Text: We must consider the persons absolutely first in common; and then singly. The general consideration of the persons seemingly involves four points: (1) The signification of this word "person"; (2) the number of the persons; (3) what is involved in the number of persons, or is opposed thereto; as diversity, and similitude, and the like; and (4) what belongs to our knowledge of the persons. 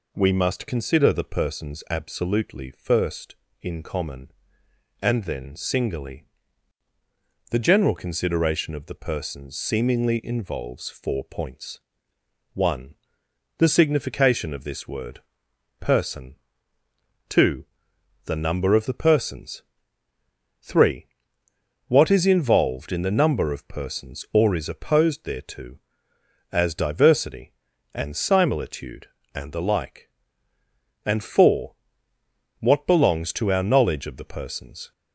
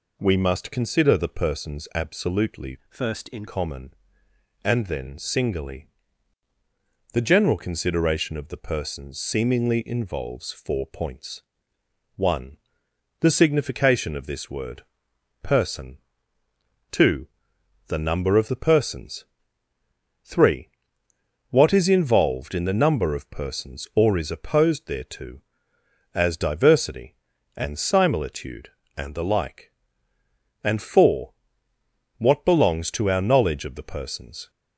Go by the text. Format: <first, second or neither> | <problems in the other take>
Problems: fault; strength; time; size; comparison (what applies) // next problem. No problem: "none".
first | changes voice from "first" to "in"; from 2.8 to 3.4 s; 0.6 s long // pauses between "word" and "person"; noticeable; at 14.8 s; 0.58 s long; noticeable in the first